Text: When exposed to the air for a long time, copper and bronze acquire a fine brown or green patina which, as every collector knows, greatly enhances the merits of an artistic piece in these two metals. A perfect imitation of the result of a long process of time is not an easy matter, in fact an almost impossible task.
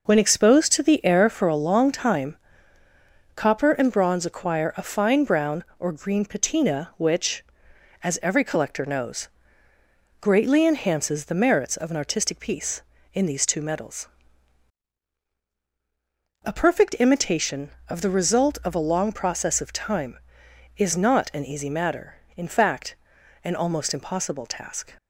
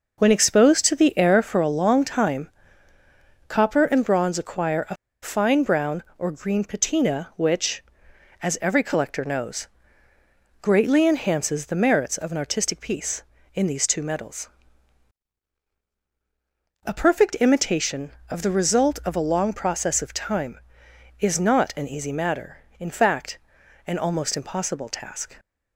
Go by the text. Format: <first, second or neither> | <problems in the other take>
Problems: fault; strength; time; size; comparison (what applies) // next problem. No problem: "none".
first | pauses between "a" and "fine"; slight; at 4.9 s; 0.27 s long // pauses between "fact" and "an"; noticeable; at 23.3 s; 0.48 s long; noticeable in the first